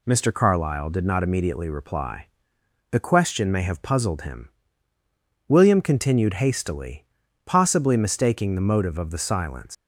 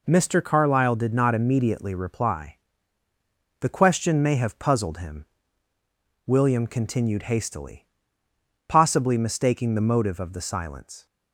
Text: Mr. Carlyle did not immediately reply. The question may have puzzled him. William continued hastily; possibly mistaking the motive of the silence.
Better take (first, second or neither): second